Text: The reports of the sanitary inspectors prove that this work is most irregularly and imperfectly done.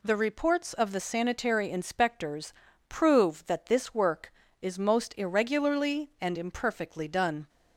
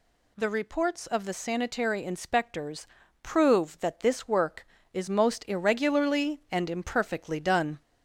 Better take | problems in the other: first | gets louder; slight; throughout; 2 dB // pauses between "inspectors" and "prove"; slight; at 2.8 s; 0.34 s long; slight in the first

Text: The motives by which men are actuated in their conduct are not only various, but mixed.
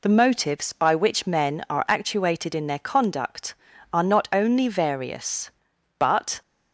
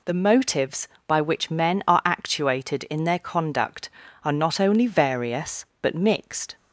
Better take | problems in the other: second | stops before "mixed"; at 6.4 s

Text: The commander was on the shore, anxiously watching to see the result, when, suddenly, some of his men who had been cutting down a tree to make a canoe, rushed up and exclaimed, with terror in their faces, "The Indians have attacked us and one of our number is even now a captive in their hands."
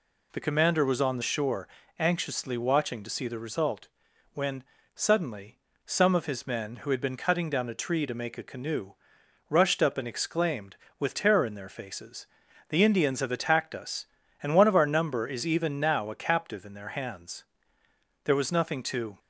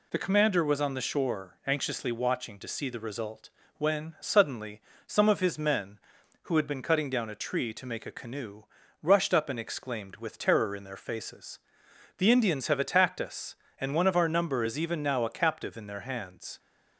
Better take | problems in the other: second | goes on to say "There was nothing to"; noticeable; from 18.2 s on; 0.94 s long

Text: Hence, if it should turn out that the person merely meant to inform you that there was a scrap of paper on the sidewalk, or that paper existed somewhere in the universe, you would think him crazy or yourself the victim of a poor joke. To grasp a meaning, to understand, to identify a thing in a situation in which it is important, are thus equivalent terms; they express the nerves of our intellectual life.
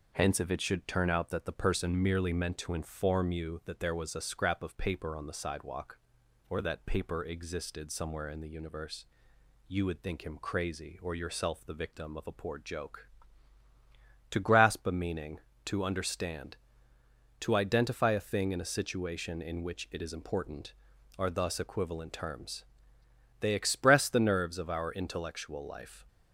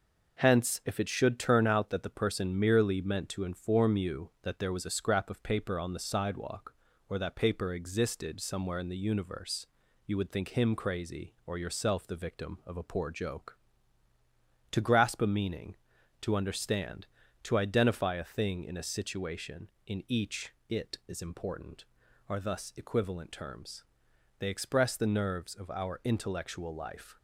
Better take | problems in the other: first | says "each" for "which"; at 20.0 s

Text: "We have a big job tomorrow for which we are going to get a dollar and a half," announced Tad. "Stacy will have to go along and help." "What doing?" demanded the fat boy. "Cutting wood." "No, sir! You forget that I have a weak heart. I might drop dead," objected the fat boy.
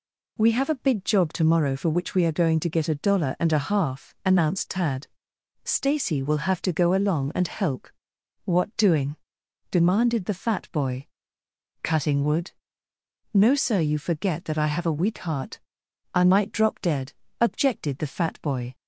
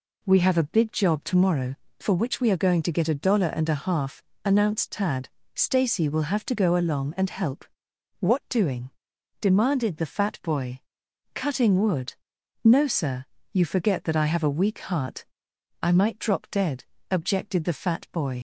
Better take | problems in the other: first | leaves "boy" unfinished; at 18.3 s; 60 ms

